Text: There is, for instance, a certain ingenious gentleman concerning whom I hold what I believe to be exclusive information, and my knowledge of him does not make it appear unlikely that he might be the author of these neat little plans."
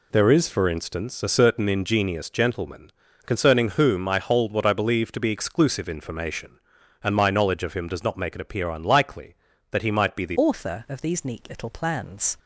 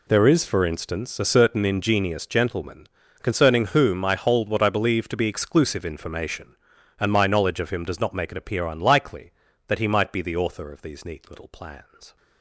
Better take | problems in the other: second | pauses between "gentleman" and "concerning"; slight; at 2.9 s; 0.34 s long; slight in the second // changes voice at "author"; from 10.3 s on; 2.0 s long

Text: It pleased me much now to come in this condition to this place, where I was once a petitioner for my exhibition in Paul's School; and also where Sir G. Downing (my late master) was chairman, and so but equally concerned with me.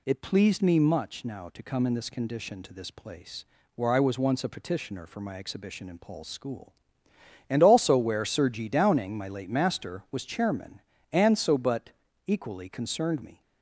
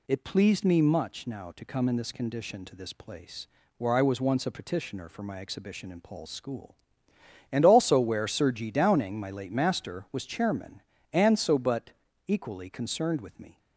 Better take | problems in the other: second | pauses between "but" and "equally"; slight; at 11.8 s; 0.36 s long; slight in the second // skips "with"; at 13.2 s

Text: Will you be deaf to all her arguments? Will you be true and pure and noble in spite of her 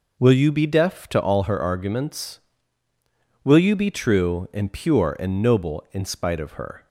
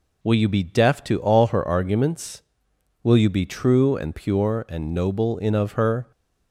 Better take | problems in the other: first | skips "spite"; at 5.5 s

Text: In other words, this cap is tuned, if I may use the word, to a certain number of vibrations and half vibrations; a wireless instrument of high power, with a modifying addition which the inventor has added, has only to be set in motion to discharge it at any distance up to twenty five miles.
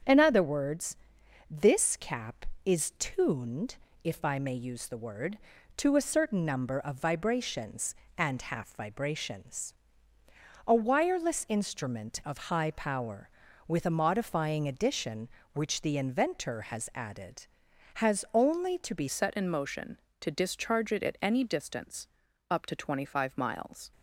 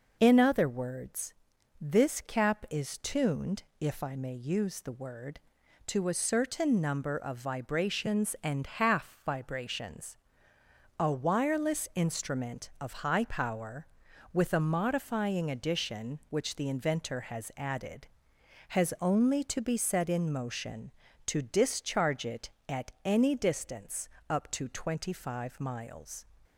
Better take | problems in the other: second | starts louder than the rest; strong; until 1.5 s; 7.5 dB // changes voice at "set"; from 19.0 s on; 4.9 s long // pauses between "distance" and "up"; at 22.0 s; 0.40 s long; slight in the second

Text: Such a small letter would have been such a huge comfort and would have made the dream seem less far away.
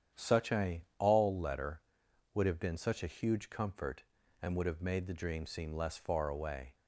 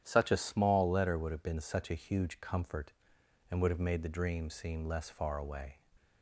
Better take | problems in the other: second | starts louder than the rest; strong; until 1.2 s; 9 dB; strong in the second // says "all" for "small"; at 0.9 s

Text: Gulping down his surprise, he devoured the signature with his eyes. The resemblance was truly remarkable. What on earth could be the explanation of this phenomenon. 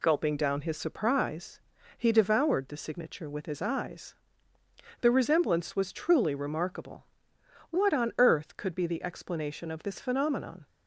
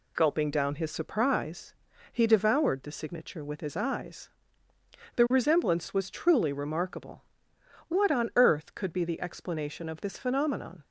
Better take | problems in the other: neither | none

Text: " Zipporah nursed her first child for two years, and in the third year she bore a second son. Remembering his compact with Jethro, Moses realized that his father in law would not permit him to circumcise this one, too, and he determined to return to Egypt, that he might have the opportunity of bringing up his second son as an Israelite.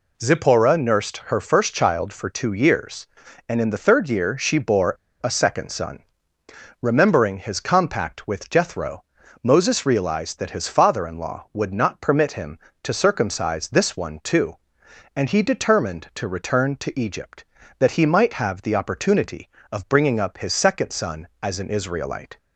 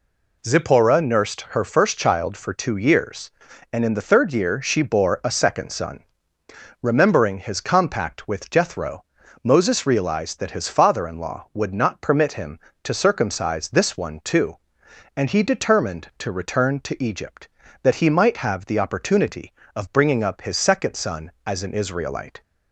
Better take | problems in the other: second | pauses between "bore" and "a"; slight; at 4.9 s; 0.25 s long

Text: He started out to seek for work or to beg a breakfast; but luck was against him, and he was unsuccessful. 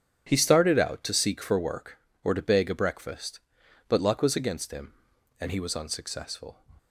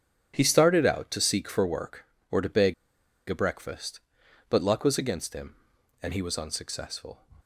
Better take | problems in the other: first | starts louder than the rest; strong; until 1.3 s; 8.5 dB; strong in the first // pauses between "beg" and "a"; noticeable; at 2.7 s; 0.55 s long

